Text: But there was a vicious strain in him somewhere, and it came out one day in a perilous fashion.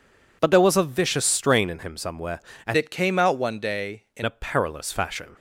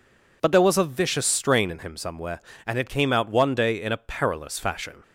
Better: second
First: changes voice from "it" to "in"; from 2.7 to 4.2 s; 1.5 s long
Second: none

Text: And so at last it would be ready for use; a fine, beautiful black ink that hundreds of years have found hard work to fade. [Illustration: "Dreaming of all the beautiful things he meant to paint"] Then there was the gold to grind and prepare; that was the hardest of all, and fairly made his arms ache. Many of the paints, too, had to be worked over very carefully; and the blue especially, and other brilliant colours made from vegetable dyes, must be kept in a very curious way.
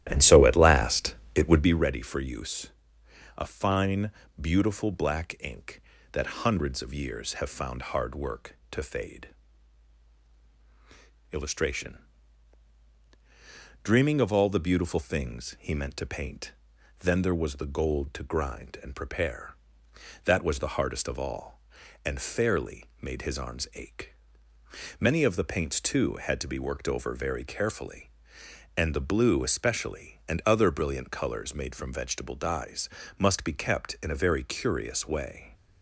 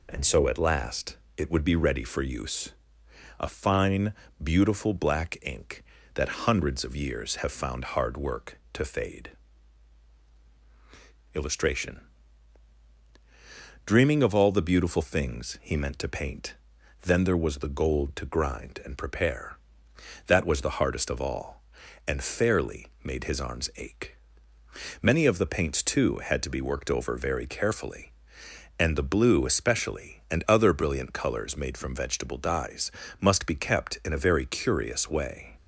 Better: second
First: starts louder than the rest; strong; until 1.9 s; 12.5 dB // pauses between "last" and "it"; slight; at 1.1 s; 0.22 s long // pauses between "paint" and "Then"; noticeable; at 16.5 s; 0.48 s long // pauses between "fairly" and "made"; slight; at 22.8 s; 0.16 s long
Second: pauses between "last" and "it"; slight; at 1.1 s; 0.22 s long // pauses between "paint" and "Then"; noticeable; at 16.5 s; 0.48 s long // pauses between "fairly" and "made"; slight; at 22.8 s; 0.16 s long

